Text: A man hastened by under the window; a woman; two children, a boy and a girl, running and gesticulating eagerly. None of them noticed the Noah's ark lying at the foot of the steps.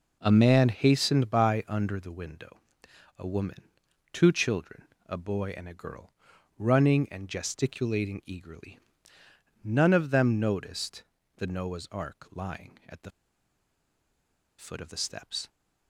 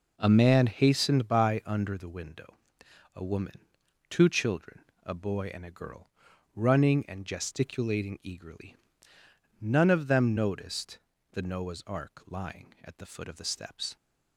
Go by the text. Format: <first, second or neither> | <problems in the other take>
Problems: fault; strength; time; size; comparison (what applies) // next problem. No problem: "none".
second | pauses between "noticed" and "the"; slight; at 11.0 s; 0.34 s long; slight in the second // pauses between "the" and "foot"; strong; at 13.1 s; 1.4 s long